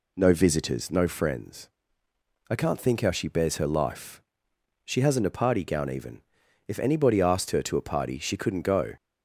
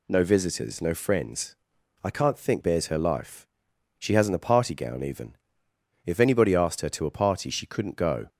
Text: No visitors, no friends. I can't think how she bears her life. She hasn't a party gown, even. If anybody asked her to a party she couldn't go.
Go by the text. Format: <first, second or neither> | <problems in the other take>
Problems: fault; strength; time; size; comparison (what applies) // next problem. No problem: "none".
first | skips "how she"; at 2.6 s